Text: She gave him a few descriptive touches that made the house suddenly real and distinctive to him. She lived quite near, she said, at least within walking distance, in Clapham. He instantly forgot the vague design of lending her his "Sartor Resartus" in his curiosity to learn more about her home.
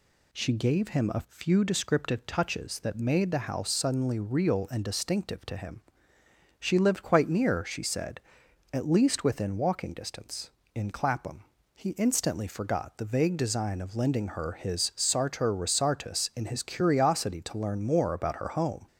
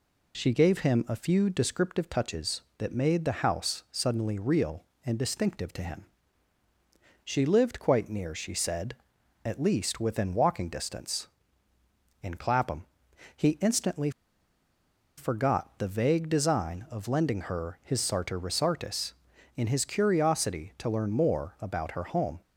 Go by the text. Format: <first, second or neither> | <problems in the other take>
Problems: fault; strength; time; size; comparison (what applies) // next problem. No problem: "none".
first | pauses between "instantly" and "forgot"; at 14.0 s; 1.0 s long